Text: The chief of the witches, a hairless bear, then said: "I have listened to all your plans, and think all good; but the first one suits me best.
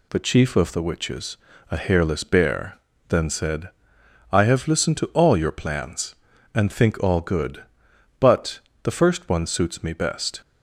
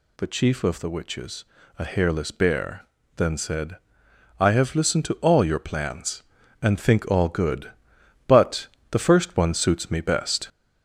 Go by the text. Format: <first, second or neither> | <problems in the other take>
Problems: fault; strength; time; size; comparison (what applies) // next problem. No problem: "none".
first | gets louder; throughout; 4 dB // pauses between "but" and "the"; slight; at 8.6 s; 0.26 s long; slight in the first